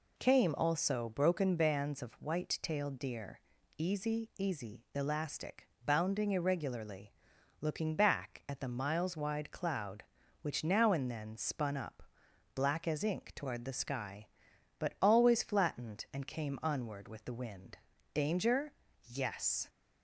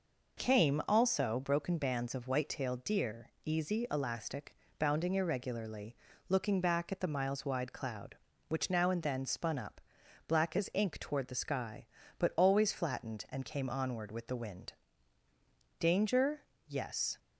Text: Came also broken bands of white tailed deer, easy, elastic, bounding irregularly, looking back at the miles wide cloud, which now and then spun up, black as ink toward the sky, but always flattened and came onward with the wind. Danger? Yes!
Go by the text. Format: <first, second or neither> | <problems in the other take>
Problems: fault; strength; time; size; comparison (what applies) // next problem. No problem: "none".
second | says "easy" twice; at 4.3 s